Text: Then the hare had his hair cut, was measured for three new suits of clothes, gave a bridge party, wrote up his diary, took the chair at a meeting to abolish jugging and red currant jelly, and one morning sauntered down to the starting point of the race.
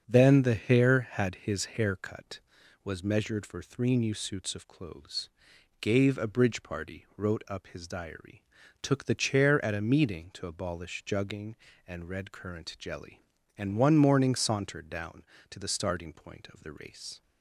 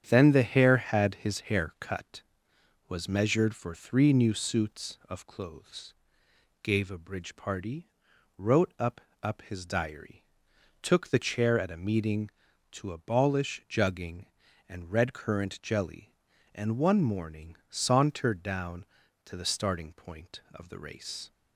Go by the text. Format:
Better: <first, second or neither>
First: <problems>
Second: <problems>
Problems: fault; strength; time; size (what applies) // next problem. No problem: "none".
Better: first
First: starts louder than the rest; until 1.0 s; 7 dB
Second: starts louder than the rest; strong; until 1.0 s; 8.5 dB // says "up" twice; at 9.2 s